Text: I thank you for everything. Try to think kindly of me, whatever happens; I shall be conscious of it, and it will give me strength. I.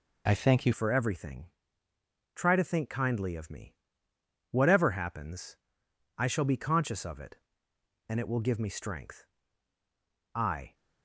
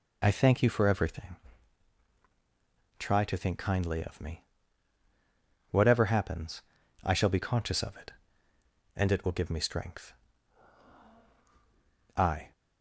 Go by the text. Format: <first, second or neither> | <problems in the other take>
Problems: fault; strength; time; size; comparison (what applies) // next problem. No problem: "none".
second | changes voice at "for"; from 0.7 s on; 10.0 s long